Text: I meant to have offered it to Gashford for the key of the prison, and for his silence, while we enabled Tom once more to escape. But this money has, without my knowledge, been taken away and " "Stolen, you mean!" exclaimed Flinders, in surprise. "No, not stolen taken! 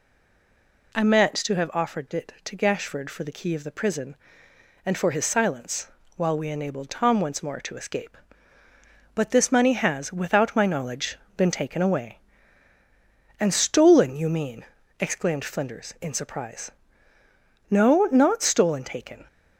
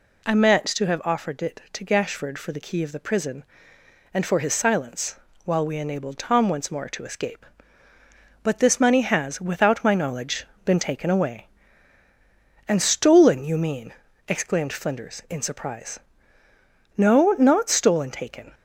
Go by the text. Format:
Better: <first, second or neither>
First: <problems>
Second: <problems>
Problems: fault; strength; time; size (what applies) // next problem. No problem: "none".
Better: second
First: stays silent before the first word; slight; until 0.9 s; 0.9 s long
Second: none